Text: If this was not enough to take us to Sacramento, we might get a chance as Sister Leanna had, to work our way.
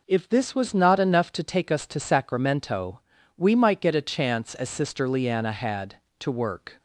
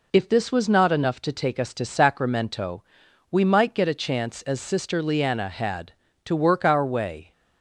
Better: second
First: stops before "our way"; at 6.7 s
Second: none

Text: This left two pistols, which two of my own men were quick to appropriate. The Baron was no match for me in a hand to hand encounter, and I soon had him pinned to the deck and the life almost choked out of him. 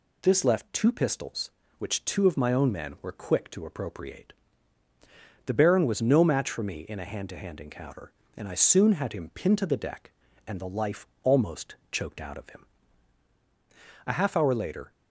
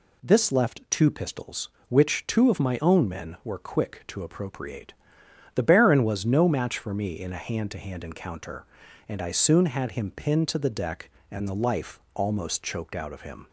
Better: second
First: pauses between "life" and "almost"; slight; at 11.0 s; 0.16 s long // pauses between "almost" and "choked"; slight; at 11.7 s; 0.16 s long // goes on to say "A half hour later"; noticeable; from 14.0 s on; 0.86 s long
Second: none

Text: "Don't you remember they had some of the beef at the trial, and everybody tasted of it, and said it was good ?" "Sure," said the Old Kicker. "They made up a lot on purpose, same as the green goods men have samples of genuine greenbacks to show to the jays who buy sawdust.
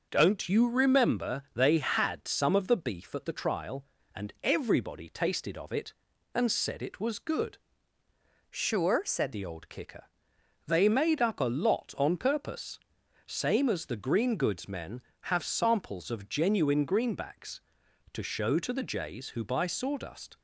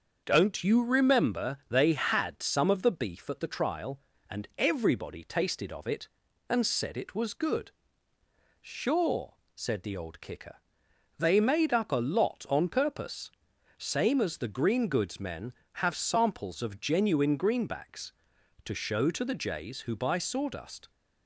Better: second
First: starts louder than the rest; until 1.1 s; 6 dB // changes voice from "Sure" to "said"; from 8.4 to 9.3 s; 0.9 s long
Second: starts louder than the rest; until 1.2 s; 6.5 dB

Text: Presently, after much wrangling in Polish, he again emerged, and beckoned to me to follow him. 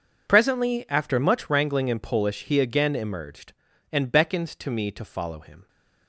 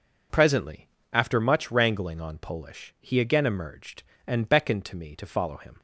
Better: first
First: none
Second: says "on" for "in"; at 2.2 s

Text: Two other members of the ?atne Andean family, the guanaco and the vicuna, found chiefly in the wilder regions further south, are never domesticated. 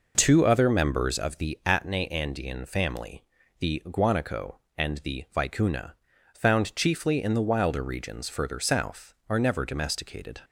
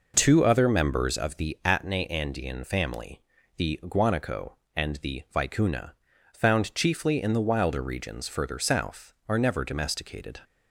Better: neither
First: none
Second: none

